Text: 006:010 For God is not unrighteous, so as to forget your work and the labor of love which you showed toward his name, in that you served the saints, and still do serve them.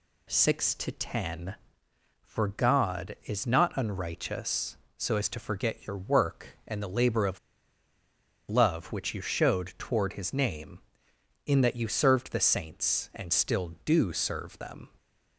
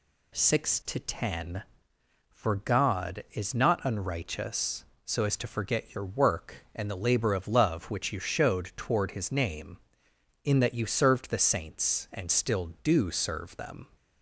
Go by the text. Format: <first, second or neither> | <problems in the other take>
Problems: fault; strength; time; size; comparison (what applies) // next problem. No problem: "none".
second | pauses between "of" and "love"; at 7.3 s; 1.1 s long